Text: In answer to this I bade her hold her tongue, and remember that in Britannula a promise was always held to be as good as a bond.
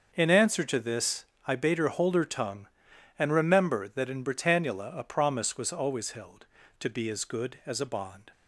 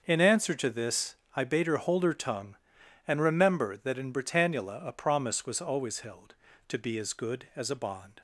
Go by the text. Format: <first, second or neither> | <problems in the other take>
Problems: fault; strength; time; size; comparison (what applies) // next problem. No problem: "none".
neither | starts louder than the rest; the same in both // pauses between "this" and "I"; slight; the same in both